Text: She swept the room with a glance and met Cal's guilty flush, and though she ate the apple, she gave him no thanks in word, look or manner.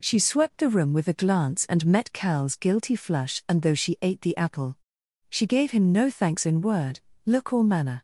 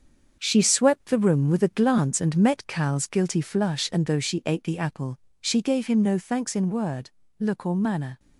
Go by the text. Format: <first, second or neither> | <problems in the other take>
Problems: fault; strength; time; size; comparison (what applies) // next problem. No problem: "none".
first | gets quieter; throughout; 7 dB